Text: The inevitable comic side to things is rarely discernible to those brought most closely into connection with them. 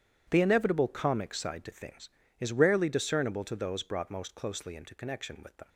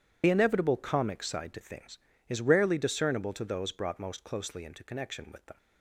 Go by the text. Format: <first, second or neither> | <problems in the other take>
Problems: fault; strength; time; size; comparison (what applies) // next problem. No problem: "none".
first | loses the start of "The"; at 0.2 s; 65 ms // starts louder than the rest; strong; until 1.2 s; 10 dB; strong in the first